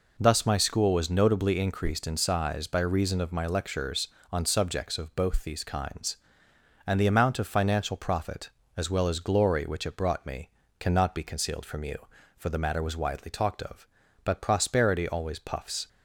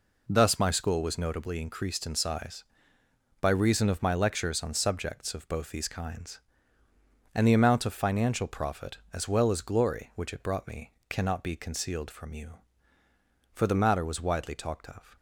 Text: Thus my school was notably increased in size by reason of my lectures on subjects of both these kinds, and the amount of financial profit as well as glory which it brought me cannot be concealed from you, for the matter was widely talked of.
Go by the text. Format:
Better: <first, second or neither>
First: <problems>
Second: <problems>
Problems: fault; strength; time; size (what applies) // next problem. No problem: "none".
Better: second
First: pauses between "me" and "cannot"; slight; at 10.4 s; 0.30 s long // goes on to say "But prosperity always puffs"; from 14.2 s on; 1.6 s long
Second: pauses between "me" and "cannot"; slight; at 10.9 s; 0.18 s long